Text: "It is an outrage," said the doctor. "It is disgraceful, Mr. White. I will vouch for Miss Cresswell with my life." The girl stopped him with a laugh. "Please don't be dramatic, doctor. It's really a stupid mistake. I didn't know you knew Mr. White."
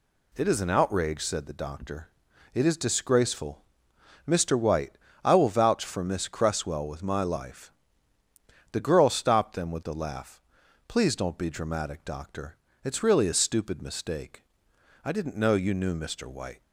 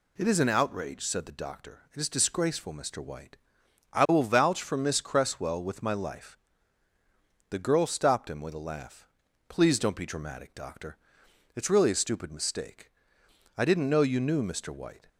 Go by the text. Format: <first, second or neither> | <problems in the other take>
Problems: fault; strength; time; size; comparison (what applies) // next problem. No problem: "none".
second | says "them" for "him"; at 9.5 s